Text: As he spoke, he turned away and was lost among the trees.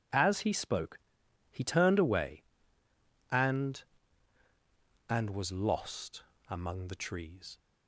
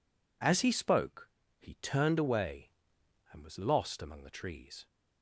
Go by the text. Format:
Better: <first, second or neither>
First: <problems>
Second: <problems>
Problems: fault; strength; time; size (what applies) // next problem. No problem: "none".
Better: second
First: says "and" twice; at 5.0 s // pauses between "lost" and "among"; slight; at 6.2 s; 0.26 s long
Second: none